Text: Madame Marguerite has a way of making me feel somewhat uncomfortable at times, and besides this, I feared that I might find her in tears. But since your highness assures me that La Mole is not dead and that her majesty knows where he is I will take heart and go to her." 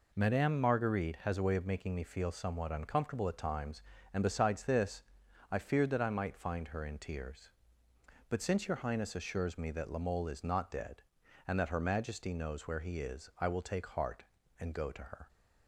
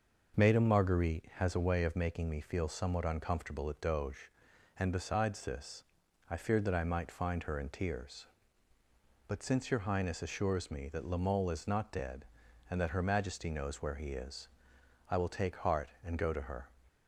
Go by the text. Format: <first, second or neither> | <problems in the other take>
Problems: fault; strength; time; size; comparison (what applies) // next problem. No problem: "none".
first | starts louder than the rest; noticeable; until 1.4 s; 6 dB // says "doge" for "times"; at 3.7 s // pauses between "is" and "I"; noticeable; at 14.4 s; 0.60 s long